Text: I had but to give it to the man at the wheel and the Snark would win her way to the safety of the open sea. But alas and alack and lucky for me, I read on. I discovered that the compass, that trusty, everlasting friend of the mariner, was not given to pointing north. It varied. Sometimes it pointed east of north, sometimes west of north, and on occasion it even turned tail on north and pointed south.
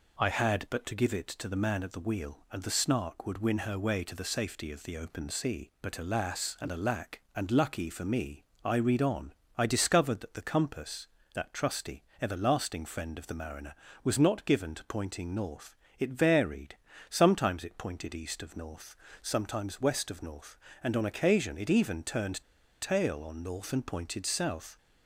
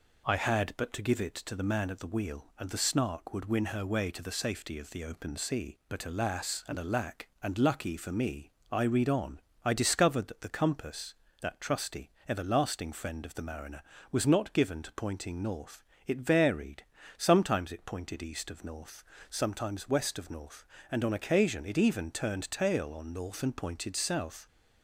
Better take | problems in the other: second | pauses between "turned" and "tail"; at 22.4 s; 0.40 s long

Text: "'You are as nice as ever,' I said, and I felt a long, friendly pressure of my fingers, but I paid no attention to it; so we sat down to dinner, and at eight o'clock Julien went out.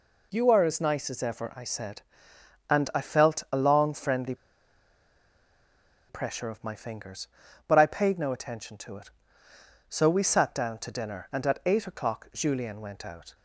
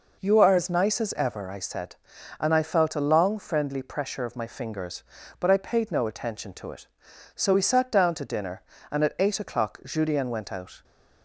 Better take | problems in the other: second | pauses between "friendly" and "pressure"; strong; at 4.3 s; 1.7 s long

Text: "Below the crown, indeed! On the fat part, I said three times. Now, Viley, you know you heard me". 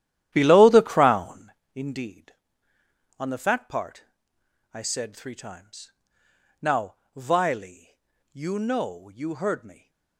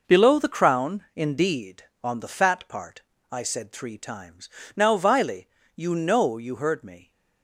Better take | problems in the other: second | starts louder than the rest; strong; until 1.5 s; 12 dB

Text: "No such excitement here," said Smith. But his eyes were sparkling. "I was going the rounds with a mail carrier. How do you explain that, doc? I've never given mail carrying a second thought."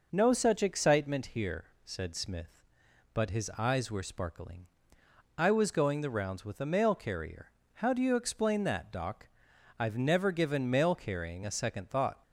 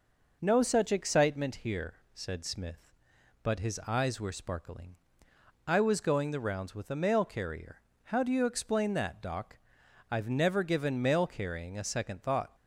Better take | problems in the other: neither | none

